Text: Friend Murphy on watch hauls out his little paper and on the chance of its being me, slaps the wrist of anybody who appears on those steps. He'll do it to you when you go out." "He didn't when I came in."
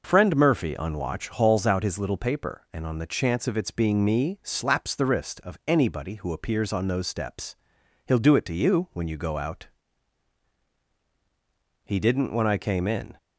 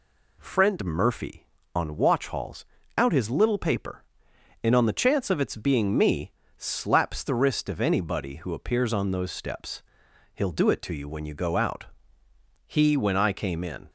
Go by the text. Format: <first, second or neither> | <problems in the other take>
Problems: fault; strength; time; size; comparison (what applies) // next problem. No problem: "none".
first | pauses between "hauls" and "out"; slight; at 2.6 s; 0.32 s long // skips "didn't"; at 12.9 s